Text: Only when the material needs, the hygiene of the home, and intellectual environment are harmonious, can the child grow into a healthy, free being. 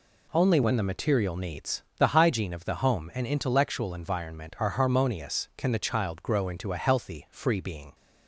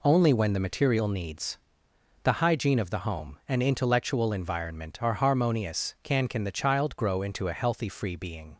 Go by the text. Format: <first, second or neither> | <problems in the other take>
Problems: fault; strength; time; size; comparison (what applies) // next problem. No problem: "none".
first | says "can" twice; at 6.2 s